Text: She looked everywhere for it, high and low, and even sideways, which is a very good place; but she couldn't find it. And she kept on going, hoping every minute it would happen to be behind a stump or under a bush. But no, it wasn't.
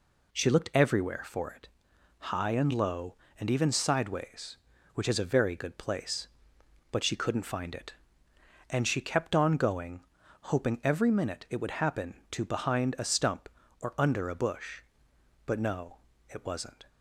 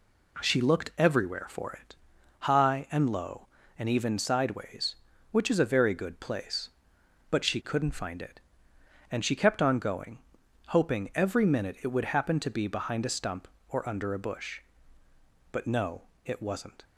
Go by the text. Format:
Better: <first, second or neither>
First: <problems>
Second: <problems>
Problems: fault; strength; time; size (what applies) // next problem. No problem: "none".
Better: second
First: skips "be"; at 12.4 s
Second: none